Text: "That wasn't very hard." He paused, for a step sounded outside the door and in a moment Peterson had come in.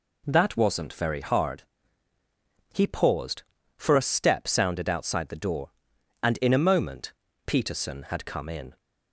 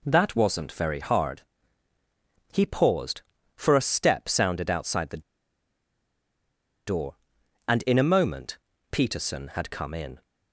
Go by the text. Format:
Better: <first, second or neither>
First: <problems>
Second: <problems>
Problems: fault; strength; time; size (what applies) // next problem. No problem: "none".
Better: first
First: pauses between "moment" and "Peterson"; slight; at 7.1 s; 0.34 s long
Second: pauses between "the" and "door"; strong; at 5.2 s; 1.6 s long // pauses between "moment" and "Peterson"; slight; at 8.5 s; 0.34 s long